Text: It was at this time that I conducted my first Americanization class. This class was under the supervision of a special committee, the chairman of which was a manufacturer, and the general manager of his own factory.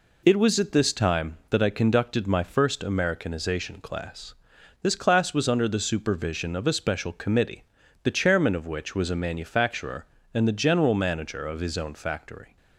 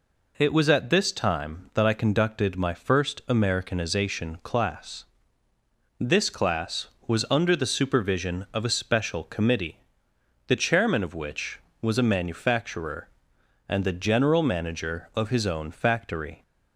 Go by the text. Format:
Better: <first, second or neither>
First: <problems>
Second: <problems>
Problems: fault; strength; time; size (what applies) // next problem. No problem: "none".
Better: neither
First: none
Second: none